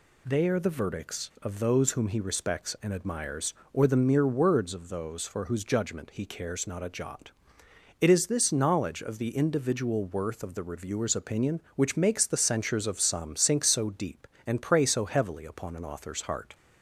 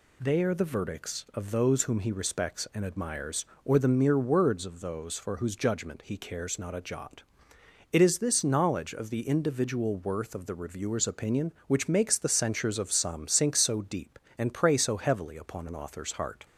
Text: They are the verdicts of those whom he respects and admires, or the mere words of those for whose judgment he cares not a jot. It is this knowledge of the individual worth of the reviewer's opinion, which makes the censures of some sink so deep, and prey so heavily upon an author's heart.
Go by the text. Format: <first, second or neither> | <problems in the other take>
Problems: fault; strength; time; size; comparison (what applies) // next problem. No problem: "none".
neither | none